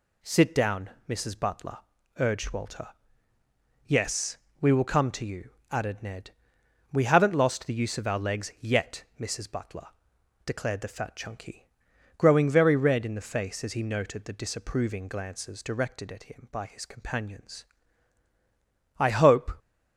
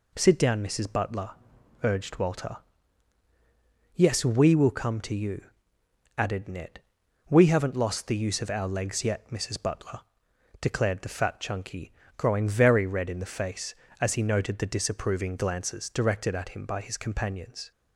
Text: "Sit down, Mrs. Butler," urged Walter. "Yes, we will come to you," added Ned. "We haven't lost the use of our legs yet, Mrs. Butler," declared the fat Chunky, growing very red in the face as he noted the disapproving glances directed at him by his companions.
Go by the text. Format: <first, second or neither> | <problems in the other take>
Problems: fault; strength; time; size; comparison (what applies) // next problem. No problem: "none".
second | goes on to say "I hope"; from 18.9 s on; 0.58 s long